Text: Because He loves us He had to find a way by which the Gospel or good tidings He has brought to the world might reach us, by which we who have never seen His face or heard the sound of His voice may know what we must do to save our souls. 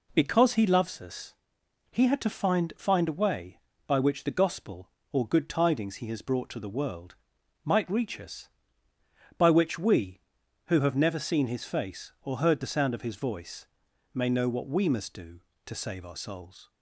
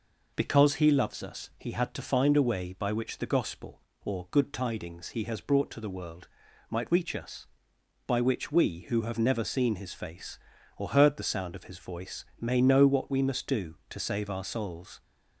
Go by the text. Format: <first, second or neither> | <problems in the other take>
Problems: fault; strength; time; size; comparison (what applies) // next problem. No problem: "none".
second | pauses between "us" and "He"; noticeable; at 1.3 s; 0.58 s long // says "find" twice; at 2.7 s // pauses between "world" and "might"; noticeable; at 7.1 s; 0.48 s long; also in the second // pauses between "voice" and "may"; noticeable; at 13.6 s; 0.46 s long; slight in the second